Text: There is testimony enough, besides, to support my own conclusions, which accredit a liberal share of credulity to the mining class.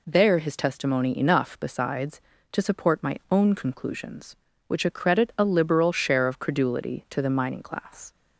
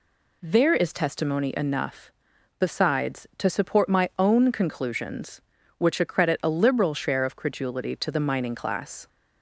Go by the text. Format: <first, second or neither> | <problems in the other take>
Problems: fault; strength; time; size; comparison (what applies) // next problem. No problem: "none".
second | says "his" for "is"; at 0.3 s